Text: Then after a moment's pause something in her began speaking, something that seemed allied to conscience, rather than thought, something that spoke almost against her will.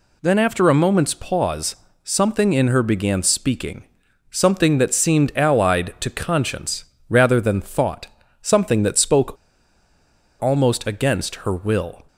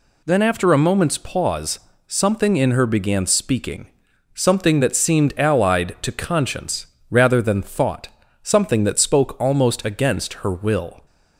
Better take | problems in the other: second | pauses between "pause" and "something"; slight; at 1.7 s; 0.28 s long; slight in the second // pauses between "spoke" and "almost"; at 9.3 s; 1.0 s long

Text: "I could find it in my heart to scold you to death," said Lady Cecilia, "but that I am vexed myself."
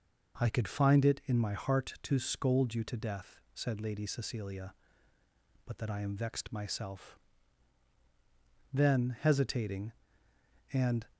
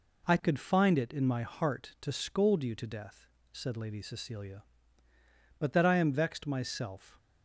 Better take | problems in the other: second | goes on to say "Then hesitating and"; strong; from 8.7 s on; 2.3 s long

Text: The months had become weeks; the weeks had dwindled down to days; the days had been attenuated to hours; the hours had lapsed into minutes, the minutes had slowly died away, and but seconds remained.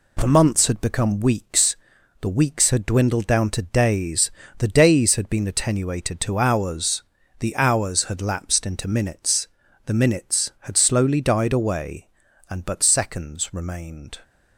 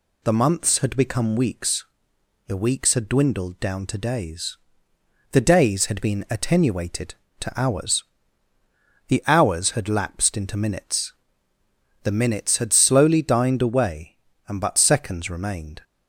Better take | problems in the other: first | says "dined" for "died"; at 13.2 s

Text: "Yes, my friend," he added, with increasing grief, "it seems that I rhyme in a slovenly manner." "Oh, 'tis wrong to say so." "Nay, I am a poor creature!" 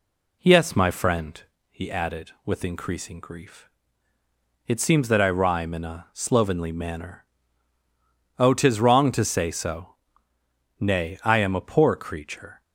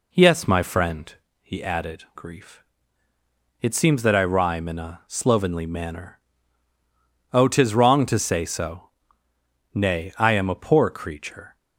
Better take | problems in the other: first | skips "with increasing"; at 2.0 s

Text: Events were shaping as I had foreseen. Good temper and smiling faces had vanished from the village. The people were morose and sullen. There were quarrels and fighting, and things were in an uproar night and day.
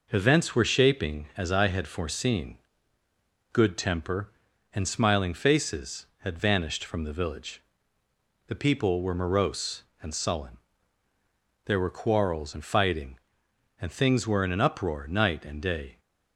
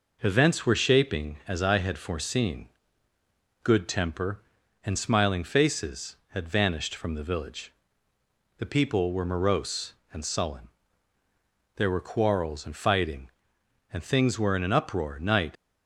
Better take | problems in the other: first | stops before "and day"; at 15.5 s

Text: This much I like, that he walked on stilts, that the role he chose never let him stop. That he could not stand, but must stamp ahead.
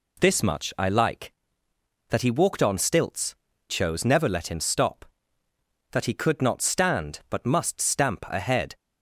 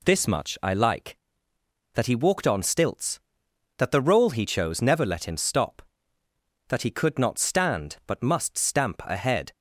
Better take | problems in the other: second | skips "that the role he"; at 3.5 s

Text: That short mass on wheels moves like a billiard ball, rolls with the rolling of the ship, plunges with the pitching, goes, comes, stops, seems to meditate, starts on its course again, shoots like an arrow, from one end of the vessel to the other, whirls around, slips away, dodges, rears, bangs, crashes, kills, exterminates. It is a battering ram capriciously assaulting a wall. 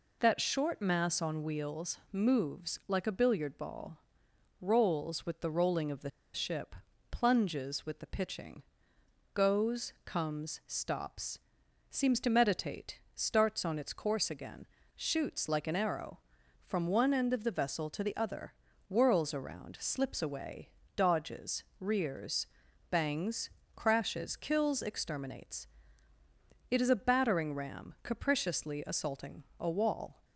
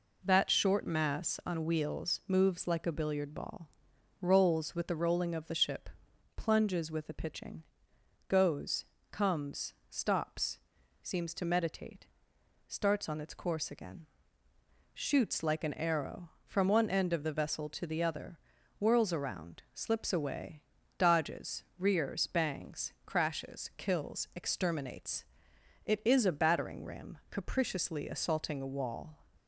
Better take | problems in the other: second | pauses between "the" and "ship"; slight; at 6.1 s; 0.24 s long // pauses between "assaulting" and "a"; slight; at 29.4 s; 0.16 s long

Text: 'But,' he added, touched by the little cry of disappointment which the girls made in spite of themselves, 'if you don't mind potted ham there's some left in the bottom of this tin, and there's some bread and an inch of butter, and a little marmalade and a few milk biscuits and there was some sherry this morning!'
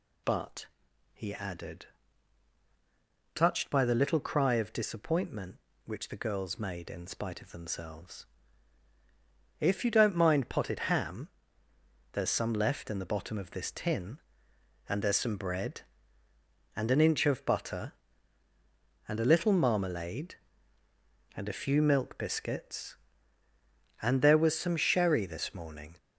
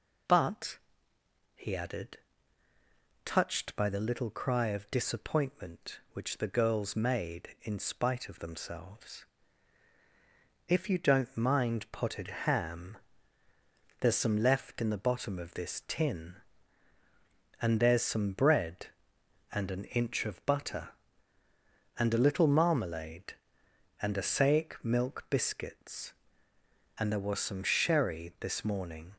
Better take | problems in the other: first | pauses between "ham" and "there's"; at 12.9 s; 1.0 s long; noticeable in the first // says "saic" for "few"; at 24.2 s

